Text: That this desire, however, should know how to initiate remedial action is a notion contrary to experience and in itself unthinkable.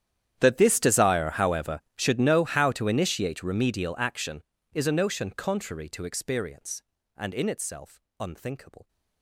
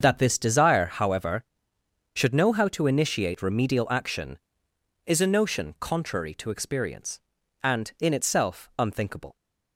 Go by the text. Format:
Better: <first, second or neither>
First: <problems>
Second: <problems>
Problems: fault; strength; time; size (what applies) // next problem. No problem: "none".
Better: second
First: gets quieter; strong; throughout; 24 dB // starts louder than the rest; strong; until 1.4 s; 10 dB // pauses between "itself" and "unthinkable"; slight; at 7.9 s; 0.20 s long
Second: starts louder than the rest; until 1.0 s; 7 dB